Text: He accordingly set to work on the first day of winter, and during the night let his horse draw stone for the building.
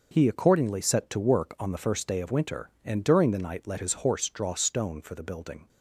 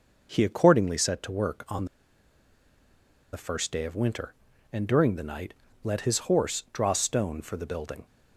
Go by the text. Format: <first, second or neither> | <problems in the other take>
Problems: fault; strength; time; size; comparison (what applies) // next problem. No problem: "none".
first | pauses between "on" and "the"; strong; at 1.8 s; 1.4 s long // pauses between "night" and "let"; slight; at 5.5 s; 0.32 s long